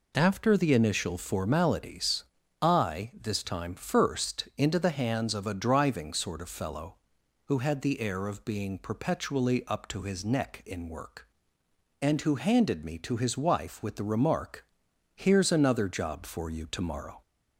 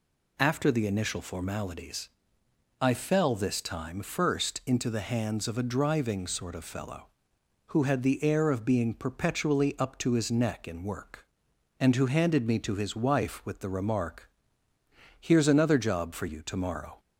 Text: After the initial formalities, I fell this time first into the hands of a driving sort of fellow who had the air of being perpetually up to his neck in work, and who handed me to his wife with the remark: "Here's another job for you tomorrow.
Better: second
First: skips "fell"; at 3.1 s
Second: none

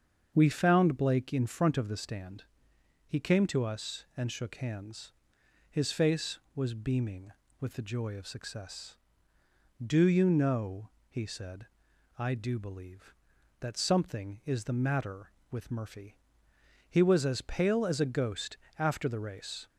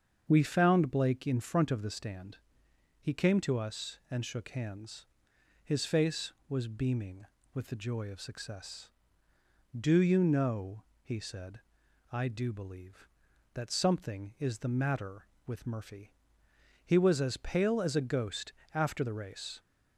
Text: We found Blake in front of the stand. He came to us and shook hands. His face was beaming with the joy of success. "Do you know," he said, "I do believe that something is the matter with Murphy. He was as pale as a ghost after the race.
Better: neither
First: starts louder than the rest; until 1.3 s; 7 dB // pauses between "ghost" and "after"; slight; at 18.5 s; 0.22 s long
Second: starts louder than the rest; until 1.3 s; 7 dB // pauses between "ghost" and "after"; slight; at 18.5 s; 0.22 s long

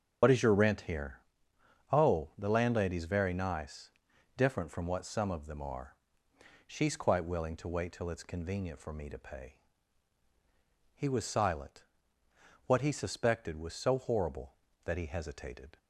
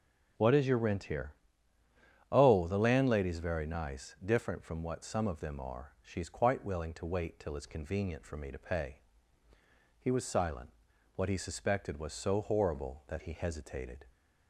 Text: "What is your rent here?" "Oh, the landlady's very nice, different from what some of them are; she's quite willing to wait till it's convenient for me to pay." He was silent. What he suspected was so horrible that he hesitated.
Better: second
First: loses the start of "What"; at 0.2 s; 50 ms // starts louder than the rest; strong; until 2.0 s; 8.5 dB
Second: none

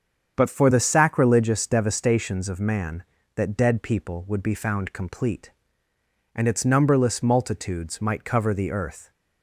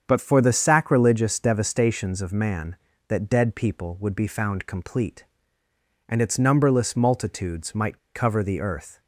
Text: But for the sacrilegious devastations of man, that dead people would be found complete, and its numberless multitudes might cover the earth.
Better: first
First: starts louder than the rest; strong; until 1.3 s; 7.5 dB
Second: starts louder than the rest; strong; until 1.0 s; 7.5 dB // pauses between "might" and "cover"; slight; at 7.9 s; 0.16 s long

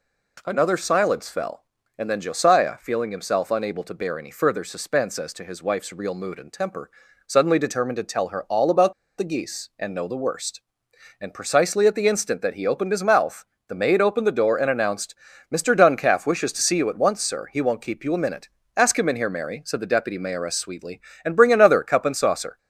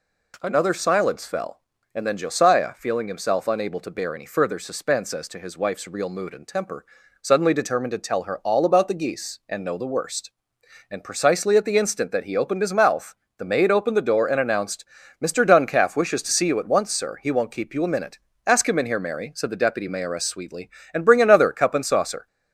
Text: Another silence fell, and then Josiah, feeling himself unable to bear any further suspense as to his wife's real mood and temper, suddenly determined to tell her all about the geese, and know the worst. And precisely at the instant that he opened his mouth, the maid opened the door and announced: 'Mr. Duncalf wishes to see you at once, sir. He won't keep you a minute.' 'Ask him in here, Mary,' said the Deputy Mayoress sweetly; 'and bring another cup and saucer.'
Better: second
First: pauses between "about" and "the"; slight; at 8.9 s; 0.25 s long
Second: none

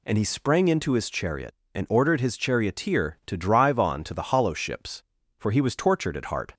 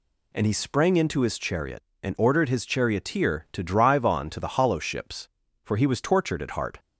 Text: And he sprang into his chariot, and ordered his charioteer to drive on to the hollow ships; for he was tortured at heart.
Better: neither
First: none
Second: none

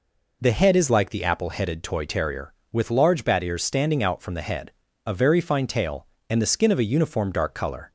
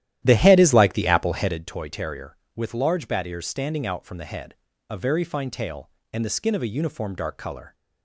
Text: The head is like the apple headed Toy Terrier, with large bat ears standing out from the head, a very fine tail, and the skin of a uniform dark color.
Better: first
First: none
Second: starts louder than the rest; strong; until 1.7 s; 12.5 dB

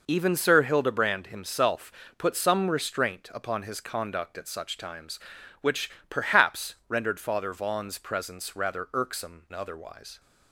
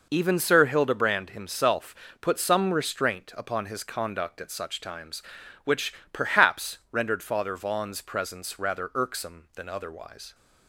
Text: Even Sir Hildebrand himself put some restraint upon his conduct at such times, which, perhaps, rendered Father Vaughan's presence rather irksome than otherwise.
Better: second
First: pauses between "himself" and "put"; slight; at 1.8 s; 0.28 s long // skips "than"; at 9.4 s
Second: pauses between "himself" and "put"; slight; at 1.9 s; 0.28 s long

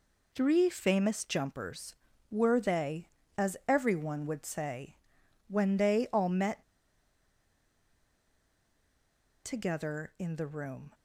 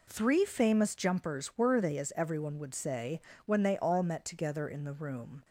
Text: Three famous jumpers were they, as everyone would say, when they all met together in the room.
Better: second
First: pauses between "met" and "together"; strong; at 6.6 s; 2.8 s long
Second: none

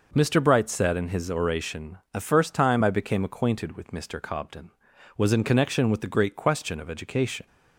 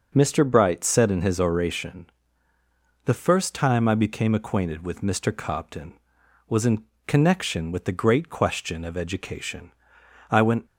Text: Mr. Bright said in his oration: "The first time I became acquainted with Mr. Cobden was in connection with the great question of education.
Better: first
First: none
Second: pauses between "in" and "connection"; slight; at 6.8 s; 0.22 s long // goes on to say "I went"; slight; from 10.3 s on; 0.34 s long

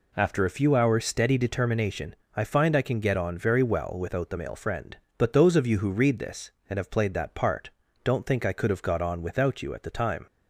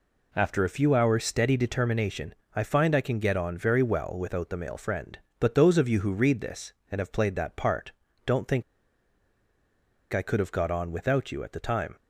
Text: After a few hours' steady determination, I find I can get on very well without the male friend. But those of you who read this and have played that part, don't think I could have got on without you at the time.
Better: first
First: none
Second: pauses between "think" and "I"; strong; at 8.6 s; 1.5 s long

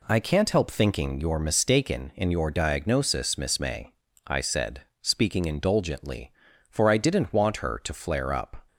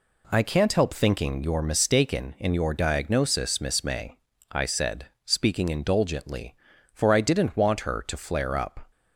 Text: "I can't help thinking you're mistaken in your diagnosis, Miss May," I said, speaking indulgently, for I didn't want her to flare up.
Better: neither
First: none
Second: none

